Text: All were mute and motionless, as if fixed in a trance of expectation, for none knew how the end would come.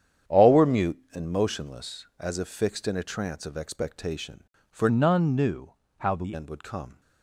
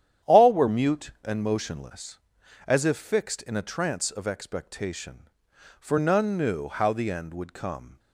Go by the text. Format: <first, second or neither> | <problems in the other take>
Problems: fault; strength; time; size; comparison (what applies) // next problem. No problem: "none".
second | starts louder than the rest; strong; until 1.4 s; 9 dB; strong in the second // changes voice from "none" to "the"; from 4.8 to 6.3 s; 1.5 s long // pauses between "knew" and "how"; slight; at 5.7 s; 0.26 s long